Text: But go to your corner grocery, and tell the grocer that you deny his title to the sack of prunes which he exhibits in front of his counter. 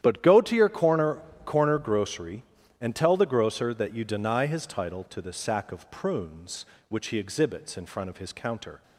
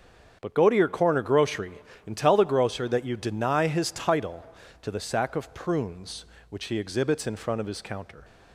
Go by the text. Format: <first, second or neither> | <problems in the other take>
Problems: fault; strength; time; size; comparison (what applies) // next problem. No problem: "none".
second | starts louder than the rest; strong; until 1.0 s; 10.5 dB; strong in the second // says "corner" twice; at 1.4 s